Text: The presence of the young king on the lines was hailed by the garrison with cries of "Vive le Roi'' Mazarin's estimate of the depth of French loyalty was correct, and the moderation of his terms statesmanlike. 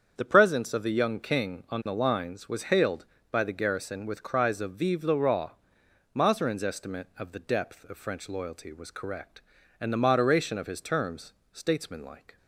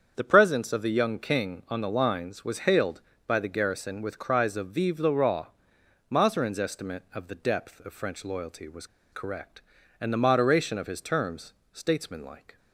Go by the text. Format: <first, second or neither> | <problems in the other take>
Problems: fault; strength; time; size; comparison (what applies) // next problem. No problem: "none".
first | starts louder than the rest; strong; until 1.1 s; 7.5 dB; strong in the first // pauses between "Roi" and "Mazarin's"; noticeable; at 5.4 s; 0.60 s long; noticeable in the first // pauses between "was" and "correct"; slight; at 8.8 s; 0.26 s long // pauses between "terms" and "statesmanlike"; slight; at 11.5 s; 0.22 s long; slight in the first